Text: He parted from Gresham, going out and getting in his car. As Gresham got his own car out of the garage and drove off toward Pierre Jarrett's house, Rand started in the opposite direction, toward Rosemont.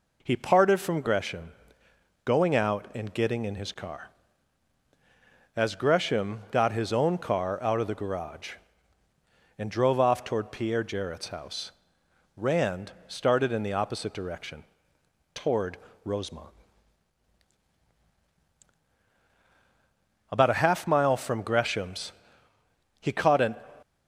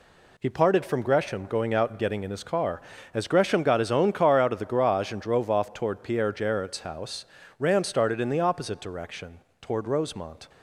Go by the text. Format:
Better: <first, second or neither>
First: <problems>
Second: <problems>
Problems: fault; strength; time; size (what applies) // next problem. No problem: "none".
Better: second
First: pauses between "toward" and "Rosemont"; slight; at 15.7 s; 0.28 s long // goes on to say "About a half mile from Gresham's he caught an"; strong; from 20.3 s on; 3.2 s long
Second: none